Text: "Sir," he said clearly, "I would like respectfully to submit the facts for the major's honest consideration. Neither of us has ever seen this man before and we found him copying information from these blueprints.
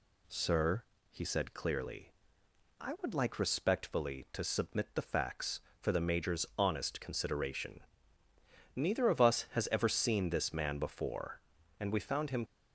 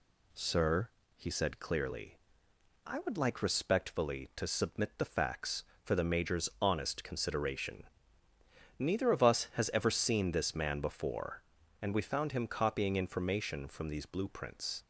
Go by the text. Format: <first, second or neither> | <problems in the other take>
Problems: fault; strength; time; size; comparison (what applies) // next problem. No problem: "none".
second | stops before "copying information from these blueprints"; at 12.4 s